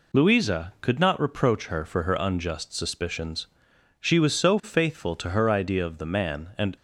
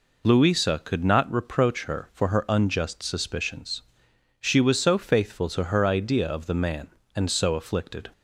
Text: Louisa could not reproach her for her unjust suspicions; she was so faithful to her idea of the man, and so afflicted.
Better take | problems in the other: second | stops before "so afflicted"; at 6.7 s

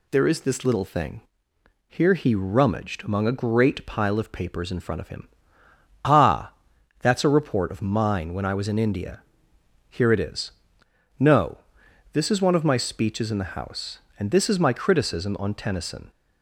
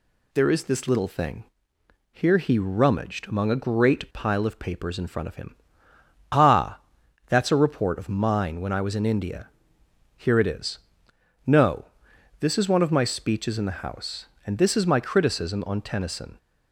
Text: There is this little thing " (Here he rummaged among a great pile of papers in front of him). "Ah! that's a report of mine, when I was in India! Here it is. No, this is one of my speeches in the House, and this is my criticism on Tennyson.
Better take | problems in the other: neither | none

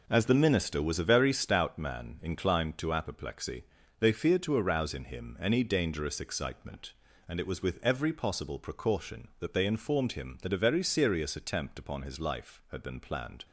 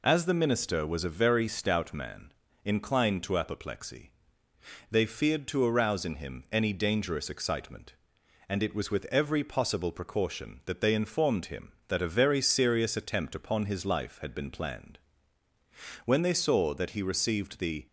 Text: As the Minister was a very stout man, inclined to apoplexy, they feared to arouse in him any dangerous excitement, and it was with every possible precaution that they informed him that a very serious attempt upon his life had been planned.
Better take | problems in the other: first | goes on to say "When they saw that he received the"; strong; from 16.0 s on; 1.8 s long

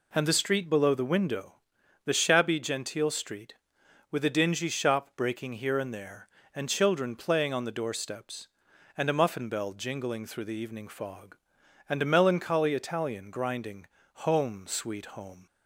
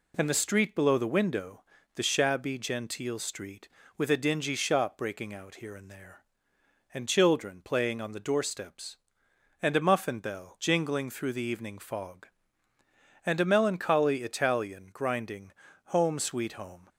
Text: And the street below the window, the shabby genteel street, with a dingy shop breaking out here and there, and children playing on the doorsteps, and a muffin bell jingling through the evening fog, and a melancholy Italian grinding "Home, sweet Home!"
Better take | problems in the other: second | skips "out"; at 5.5 s // pauses between "grinding" and "Home"; at 13.8 s; 0.42 s long; slight in the second

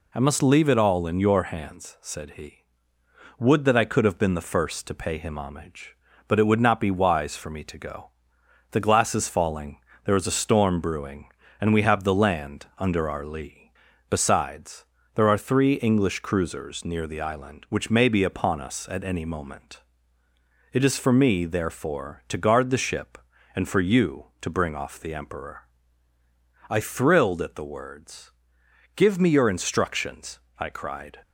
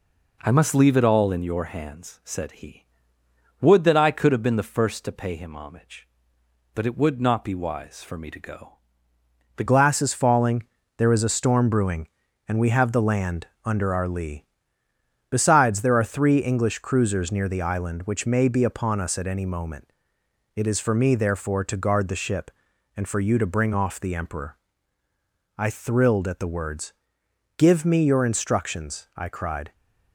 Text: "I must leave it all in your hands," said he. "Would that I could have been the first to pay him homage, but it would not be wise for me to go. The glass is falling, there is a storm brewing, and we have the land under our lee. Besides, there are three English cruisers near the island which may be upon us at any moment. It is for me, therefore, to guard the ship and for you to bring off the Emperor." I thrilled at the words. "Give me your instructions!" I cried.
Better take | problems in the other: first | changes voice at "glass"; from 9.6 s on; 20.1 s long // pauses between "land" and "under"; slight; at 13.4 s; 0.18 s long

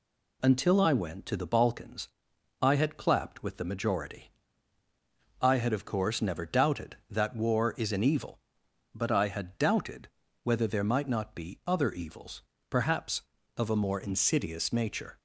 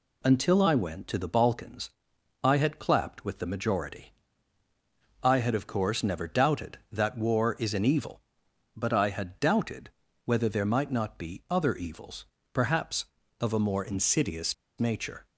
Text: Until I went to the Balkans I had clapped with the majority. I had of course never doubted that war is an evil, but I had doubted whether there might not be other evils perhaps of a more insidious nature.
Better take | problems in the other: first | pauses between "Balkans" and "I"; noticeable; at 1.8 s; 0.54 s long; noticeable in the first // pauses between "doubted" and "whether"; slight; at 9.8 s; 0.34 s long; slight in the first // pauses between "evils" and "perhaps"; slight; at 12.2 s; 0.28 s long; slight in the first // pauses between "insidious" and "nature"; slight; at 14.5 s; 0.24 s long

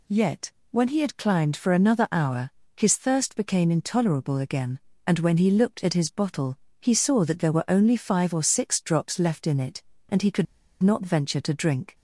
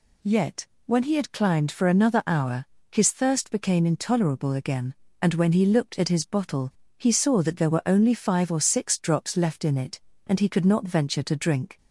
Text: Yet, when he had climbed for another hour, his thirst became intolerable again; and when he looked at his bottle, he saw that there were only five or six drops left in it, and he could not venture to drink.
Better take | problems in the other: second | pauses between "could" and "not"; slight; at 10.4 s; 0.35 s long

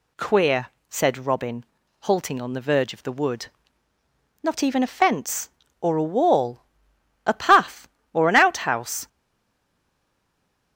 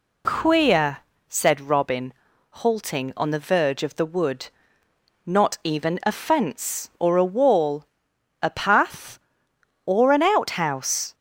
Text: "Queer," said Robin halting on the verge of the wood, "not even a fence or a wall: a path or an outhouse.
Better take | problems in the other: second | pauses between "Robin" and "halting"; slight; at 1.6 s; 0.36 s long; also in the second // stays silent after the last word; noticeable; from 9.0 s on; 1.7 s long

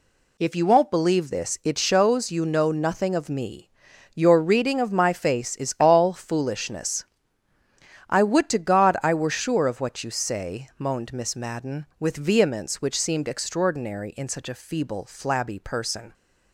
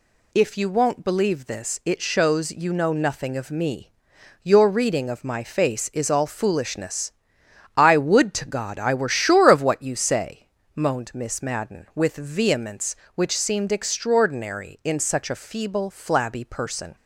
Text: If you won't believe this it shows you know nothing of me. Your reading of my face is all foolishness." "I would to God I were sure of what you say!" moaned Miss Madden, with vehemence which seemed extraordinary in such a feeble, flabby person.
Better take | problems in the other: neither | none

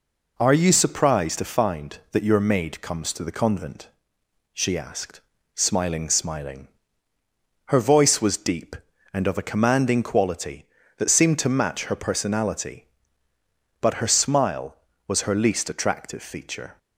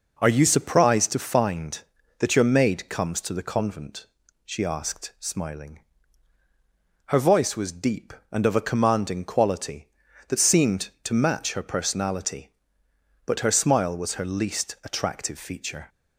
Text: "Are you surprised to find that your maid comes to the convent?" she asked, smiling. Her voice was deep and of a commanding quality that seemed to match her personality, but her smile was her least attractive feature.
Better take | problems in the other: second | says "smiling" twice; at 6.0 s

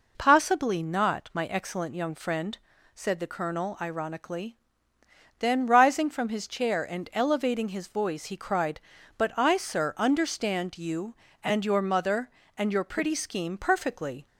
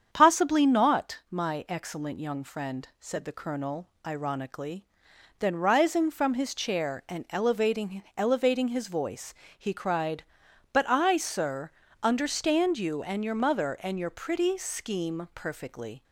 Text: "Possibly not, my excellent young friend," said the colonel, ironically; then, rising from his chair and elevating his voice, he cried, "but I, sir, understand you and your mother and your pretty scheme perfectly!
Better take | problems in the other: first | starts louder than the rest; strong; until 1.1 s; 8 dB // says "elevating" twice; at 8.1 s

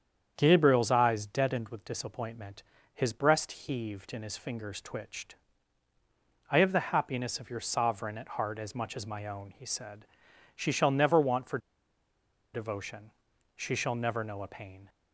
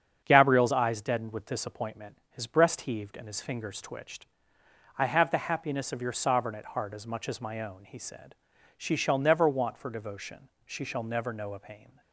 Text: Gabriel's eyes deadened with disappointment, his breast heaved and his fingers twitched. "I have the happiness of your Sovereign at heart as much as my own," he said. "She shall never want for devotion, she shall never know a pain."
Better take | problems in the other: second | starts louder than the rest; strong; until 1.3 s; 8 dB; strong in the second // pauses between "for" and "devotion"; noticeable; at 11.5 s; 0.95 s long

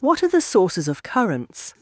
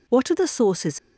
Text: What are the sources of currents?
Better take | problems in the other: first | stops before "of currents"; at 0.9 s

